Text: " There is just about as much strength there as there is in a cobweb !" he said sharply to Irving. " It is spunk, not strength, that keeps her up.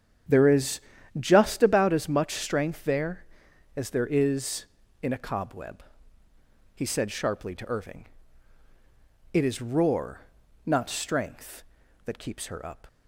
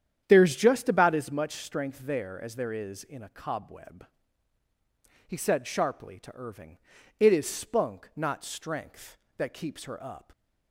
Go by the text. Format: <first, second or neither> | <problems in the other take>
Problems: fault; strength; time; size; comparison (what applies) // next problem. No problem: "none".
second | starts louder than the rest; strong; until 1.6 s; 9 dB; strong in the second // pauses between "is" and "just"; slight; at 0.8 s; 0.36 s long // says "roar" for "spunk"; at 9.6 s